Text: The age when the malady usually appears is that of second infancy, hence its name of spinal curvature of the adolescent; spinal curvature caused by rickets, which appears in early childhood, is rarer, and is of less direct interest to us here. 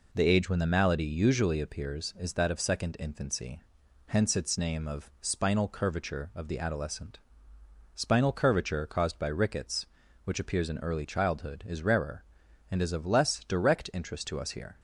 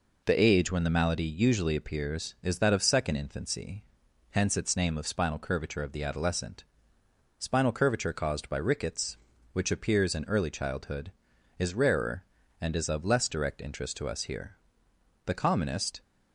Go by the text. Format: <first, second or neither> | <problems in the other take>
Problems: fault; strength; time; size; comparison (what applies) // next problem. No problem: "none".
first | goes on to say "The commonest"; noticeable; from 15.2 s on; 0.76 s long